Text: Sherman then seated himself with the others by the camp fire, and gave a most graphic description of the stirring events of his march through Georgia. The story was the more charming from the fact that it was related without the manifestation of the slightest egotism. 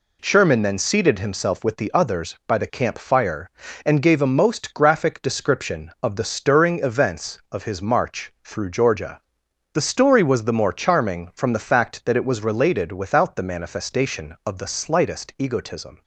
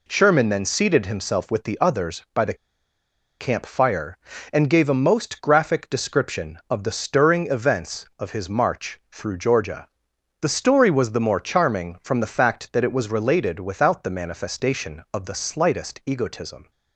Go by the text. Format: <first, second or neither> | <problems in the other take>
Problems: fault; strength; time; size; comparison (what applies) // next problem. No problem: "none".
first | pauses between "the" and "camp"; noticeable; at 2.5 s; 0.85 s long